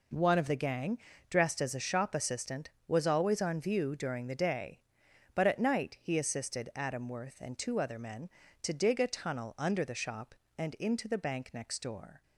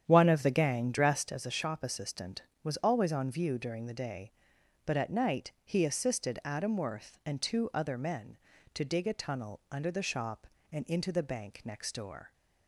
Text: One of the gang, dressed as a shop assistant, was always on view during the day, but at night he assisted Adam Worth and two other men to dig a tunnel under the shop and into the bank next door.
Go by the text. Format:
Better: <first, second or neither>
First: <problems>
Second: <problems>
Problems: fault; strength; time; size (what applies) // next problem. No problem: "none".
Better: first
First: none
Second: starts louder than the rest; strong; until 1.4 s; 9 dB